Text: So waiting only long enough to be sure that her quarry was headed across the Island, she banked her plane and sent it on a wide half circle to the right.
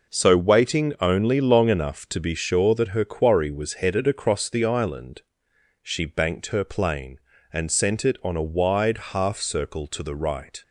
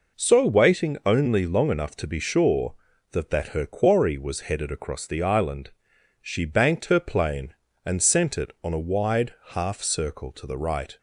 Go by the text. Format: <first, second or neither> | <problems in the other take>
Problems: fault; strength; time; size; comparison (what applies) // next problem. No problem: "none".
first | says "that" twice; at 3.3 s // pauses between "wide" and "half"; slight; at 9.3 s; 0.16 s long